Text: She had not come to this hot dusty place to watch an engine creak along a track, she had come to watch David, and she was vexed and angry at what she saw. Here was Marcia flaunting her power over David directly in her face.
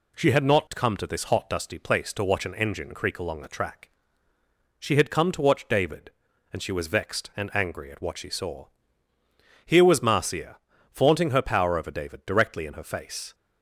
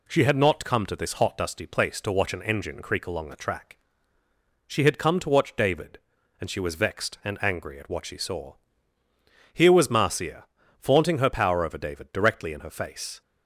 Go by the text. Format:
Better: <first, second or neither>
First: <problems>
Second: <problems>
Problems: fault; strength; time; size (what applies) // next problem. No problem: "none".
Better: neither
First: pauses between "Marcia" and "flaunting"; slight; at 10.5 s; 0.34 s long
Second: pauses between "Marcia" and "flaunting"; slight; at 10.4 s; 0.34 s long